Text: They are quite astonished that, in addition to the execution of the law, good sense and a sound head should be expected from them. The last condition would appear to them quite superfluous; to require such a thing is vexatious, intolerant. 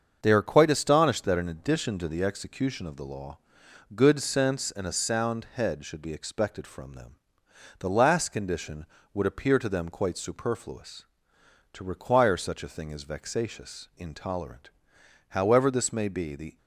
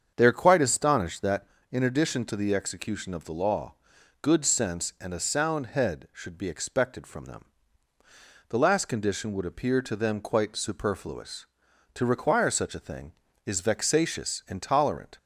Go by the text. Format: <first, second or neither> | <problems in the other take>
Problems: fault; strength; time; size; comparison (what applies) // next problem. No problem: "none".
second | starts louder than the rest; until 1.2 s; 6.5 dB; strong in the second // goes on to say "However this may be the"; noticeable; from 15.2 s on; 1.2 s long